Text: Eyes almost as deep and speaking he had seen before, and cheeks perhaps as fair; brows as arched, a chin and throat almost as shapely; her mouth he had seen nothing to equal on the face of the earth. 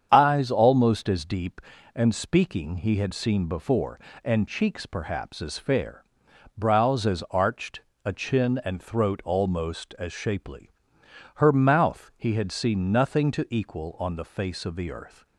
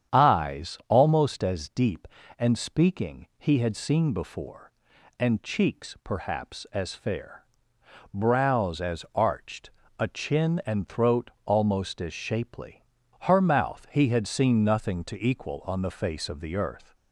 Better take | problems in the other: neither | starts louder than the rest; strong; the same in both

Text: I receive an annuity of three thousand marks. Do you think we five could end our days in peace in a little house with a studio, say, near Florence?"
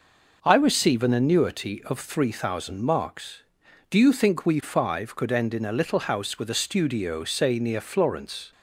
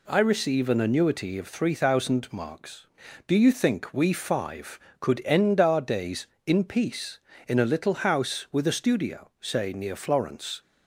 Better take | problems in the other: second | skips "our days in peace"; at 5.5 s

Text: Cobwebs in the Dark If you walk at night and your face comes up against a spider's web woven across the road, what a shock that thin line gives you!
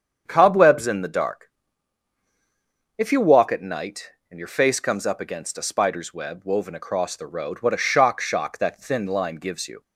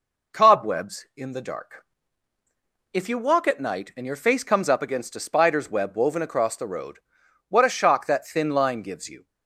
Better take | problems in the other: second | starts louder than the rest; strong; until 1.2 s; 7.5 dB // pauses between "Dark" and "If"; strong; at 1.5 s; 1.4 s long; also in the second // says "shock" twice; at 8.2 s

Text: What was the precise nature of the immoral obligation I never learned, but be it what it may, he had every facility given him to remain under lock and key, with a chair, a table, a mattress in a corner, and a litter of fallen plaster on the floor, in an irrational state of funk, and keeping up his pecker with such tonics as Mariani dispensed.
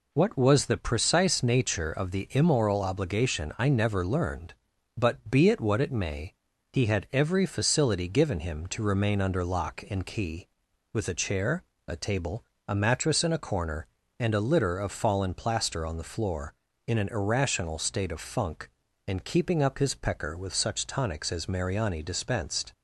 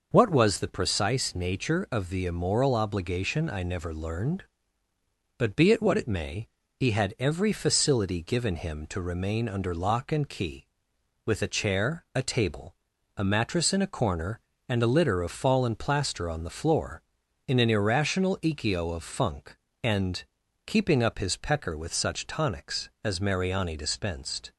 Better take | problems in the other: first | says "ikio" for "state"; at 18.4 s // pauses between "and" and "keeping"; at 20.2 s; 0.42 s long

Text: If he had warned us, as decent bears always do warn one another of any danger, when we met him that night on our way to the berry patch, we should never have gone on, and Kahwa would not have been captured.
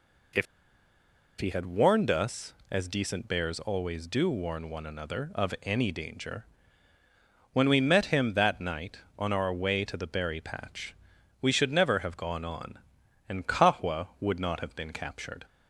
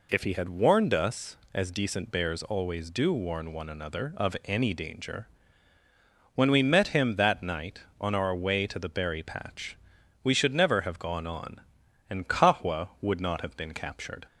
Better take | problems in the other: second | pauses between "If" and "he"; noticeable; at 0.4 s; 0.95 s long

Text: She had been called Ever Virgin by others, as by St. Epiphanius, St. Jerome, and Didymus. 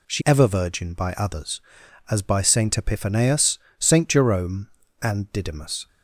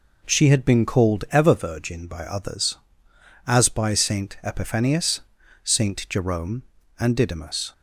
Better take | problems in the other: second | skips "had been called"; at 0.2 s

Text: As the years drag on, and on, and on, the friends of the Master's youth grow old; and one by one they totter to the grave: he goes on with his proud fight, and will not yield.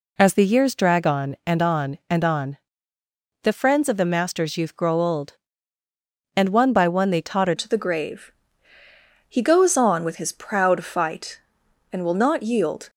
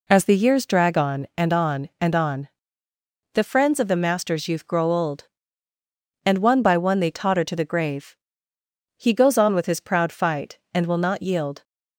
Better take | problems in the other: second | changes voice at "to"; from 7.5 s on; 5.3 s long

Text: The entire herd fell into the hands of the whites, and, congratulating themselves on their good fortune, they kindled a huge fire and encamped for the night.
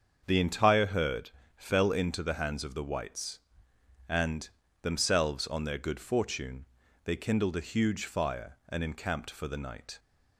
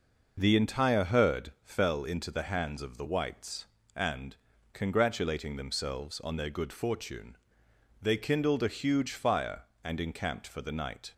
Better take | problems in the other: second | starts louder than the rest; until 1.2 s; 7 dB // pauses between "herd" and "fell"; slight; at 1.3 s; 0.24 s long // skips "congratulating"; at 4.6 s

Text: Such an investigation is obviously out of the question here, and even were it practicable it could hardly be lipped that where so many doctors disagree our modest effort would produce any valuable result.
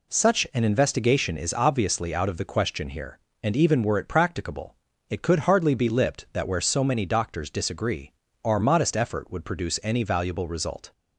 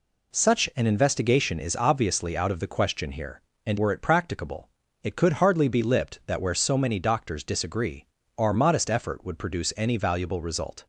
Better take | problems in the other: first | skips "even"; at 3.7 s // pauses between "practicable" and "it"; slight; at 4.6 s; 0.36 s long; slight in the first // pauses between "disagree" and "our"; slight; at 8.0 s; 0.28 s long; slight in the first

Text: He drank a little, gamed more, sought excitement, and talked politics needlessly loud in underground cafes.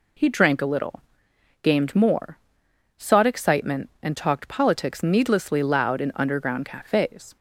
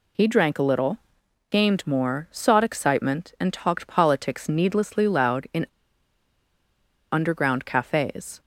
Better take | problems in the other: first | pauses between "in" and "underground"; strong; at 5.6 s; 1.4 s long

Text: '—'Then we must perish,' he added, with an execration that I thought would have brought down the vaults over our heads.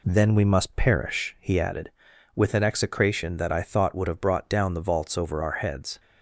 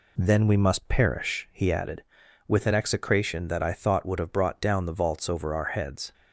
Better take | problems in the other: neither | none

